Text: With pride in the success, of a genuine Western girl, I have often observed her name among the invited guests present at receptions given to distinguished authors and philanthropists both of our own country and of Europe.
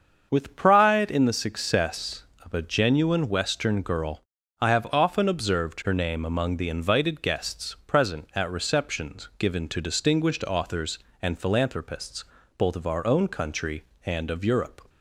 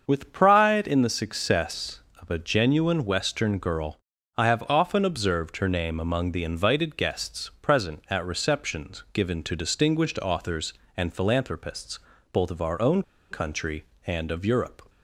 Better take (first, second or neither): first